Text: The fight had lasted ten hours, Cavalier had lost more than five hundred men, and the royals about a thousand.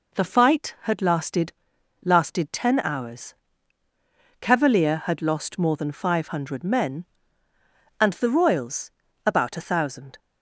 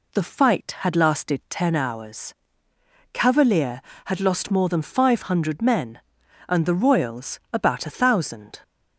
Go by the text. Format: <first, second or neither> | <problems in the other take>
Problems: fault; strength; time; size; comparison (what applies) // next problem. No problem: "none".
second | says "lasted" twice; at 2.0 s // pauses between "royals" and "about"; slight; at 8.9 s; 0.34 s long